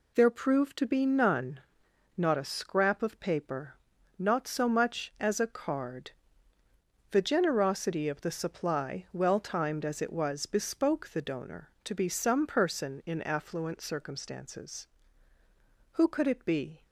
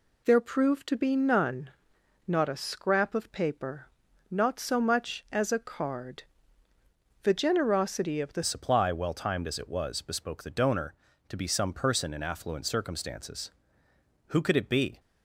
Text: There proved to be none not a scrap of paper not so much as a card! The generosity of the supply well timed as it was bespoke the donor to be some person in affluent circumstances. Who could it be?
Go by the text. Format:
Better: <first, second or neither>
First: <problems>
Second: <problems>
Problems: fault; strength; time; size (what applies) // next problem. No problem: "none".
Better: first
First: pauses between "none" and "not"; noticeable; at 1.6 s; 0.56 s long // pauses between "paper" and "not"; at 3.7 s; 0.42 s long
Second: pauses between "none" and "not"; noticeable; at 1.7 s; 0.56 s long // pauses between "paper" and "not"; at 3.8 s; 0.42 s long // changes voice at "supply"; from 8.4 s on; 6.5 s long